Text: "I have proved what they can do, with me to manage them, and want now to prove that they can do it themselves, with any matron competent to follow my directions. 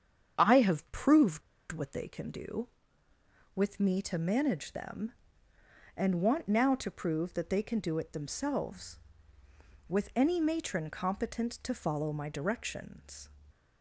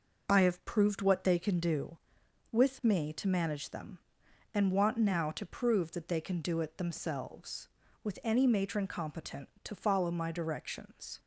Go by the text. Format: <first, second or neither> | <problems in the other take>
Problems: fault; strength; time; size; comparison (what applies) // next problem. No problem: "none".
second | starts louder than the rest; strong; until 1.4 s; 8 dB // pauses between "proved" and "what"; slight; at 1.4 s; 0.30 s long